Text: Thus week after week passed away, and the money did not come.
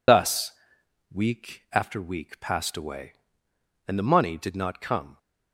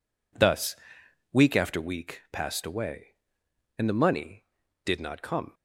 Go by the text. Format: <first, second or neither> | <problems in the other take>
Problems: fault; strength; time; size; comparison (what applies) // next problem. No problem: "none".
second | loses the start of "Thus"; at 0.0 s; 70 ms // pauses between "Thus" and "week"; noticeable; at 0.4 s; 0.64 s long; noticeable in the second